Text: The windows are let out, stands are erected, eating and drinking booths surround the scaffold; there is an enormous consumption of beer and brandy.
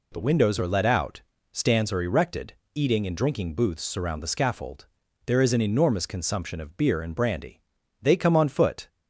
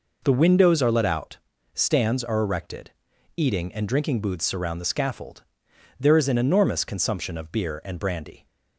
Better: second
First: goes on to say "They come on foot"; noticeable; from 8.0 s on; 0.85 s long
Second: none

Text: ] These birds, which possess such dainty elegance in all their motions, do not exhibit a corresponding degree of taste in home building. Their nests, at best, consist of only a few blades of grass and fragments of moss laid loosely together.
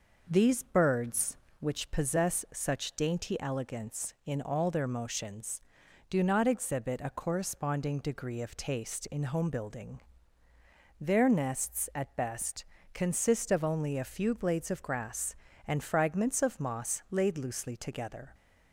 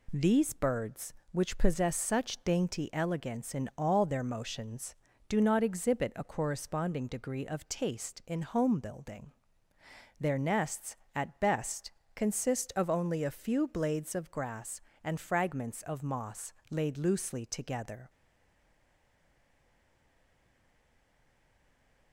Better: first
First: none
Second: pauses between "moss" and "laid"; slight; at 16.5 s; 0.18 s long // stays silent after the last word; strong; from 18.0 s on; 4.1 s long

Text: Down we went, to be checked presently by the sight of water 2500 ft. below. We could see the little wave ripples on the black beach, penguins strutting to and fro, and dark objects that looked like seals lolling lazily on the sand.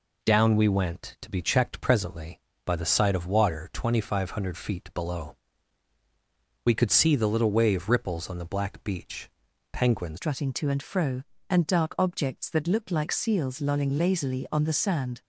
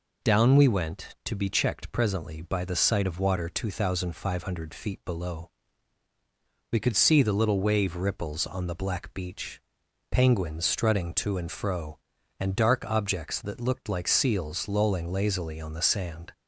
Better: second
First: changes voice at "strutting"; from 10.1 s on; 5.1 s long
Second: none

